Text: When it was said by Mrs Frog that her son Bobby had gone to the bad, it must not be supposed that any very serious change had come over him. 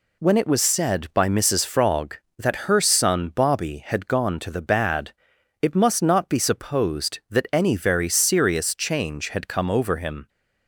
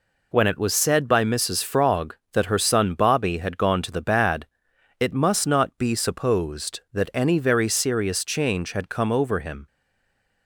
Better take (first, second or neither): first